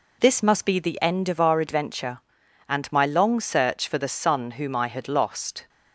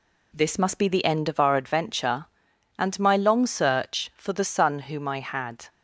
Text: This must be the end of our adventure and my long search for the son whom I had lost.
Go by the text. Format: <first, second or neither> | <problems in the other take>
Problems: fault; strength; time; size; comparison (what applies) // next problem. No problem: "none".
first | stops before "lost"; at 5.6 s